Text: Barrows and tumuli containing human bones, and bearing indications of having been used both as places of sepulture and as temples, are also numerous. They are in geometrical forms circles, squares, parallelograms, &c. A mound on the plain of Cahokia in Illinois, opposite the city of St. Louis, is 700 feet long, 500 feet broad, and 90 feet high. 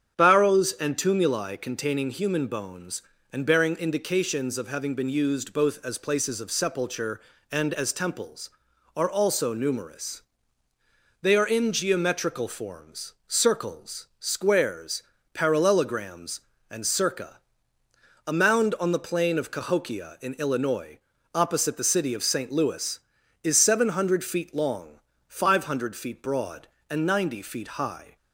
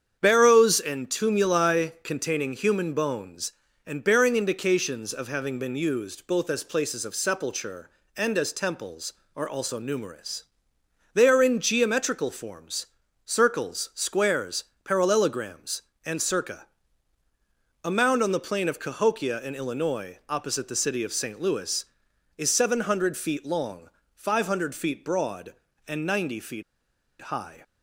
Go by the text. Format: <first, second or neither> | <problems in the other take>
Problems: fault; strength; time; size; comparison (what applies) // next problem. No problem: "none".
first | starts louder than the rest; strong; until 1.2 s; 8 dB; strong in the first // pauses between "forms" and "circles"; at 12.8 s; 0.38 s long // pauses between "feet" and "high"; noticeable; at 26.6 s; 0.59 s long